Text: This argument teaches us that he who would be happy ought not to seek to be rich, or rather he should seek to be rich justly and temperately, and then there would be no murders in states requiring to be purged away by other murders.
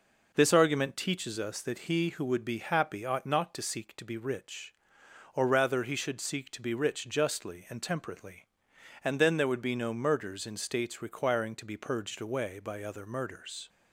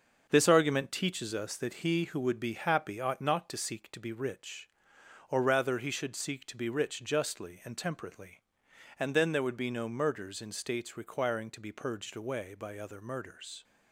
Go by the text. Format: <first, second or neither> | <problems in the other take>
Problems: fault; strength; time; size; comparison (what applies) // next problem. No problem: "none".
first | gets quieter; throughout; 7 dB